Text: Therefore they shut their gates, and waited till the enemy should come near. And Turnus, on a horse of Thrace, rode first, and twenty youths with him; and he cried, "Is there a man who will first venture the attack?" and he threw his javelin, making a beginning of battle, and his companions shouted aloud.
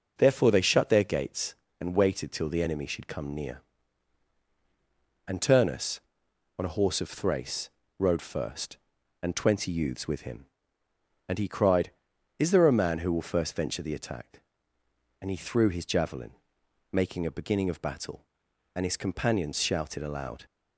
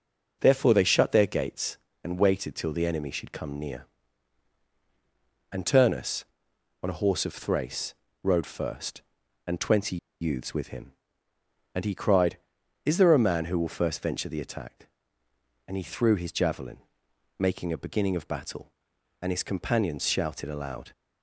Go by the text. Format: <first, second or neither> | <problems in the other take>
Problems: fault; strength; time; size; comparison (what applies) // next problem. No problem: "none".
first | pauses between "twenty" and "youths"; slight; at 9.9 s; 0.24 s long